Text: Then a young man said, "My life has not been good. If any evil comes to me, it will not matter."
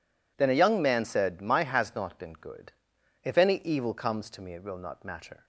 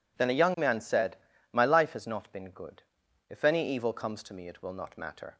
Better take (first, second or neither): second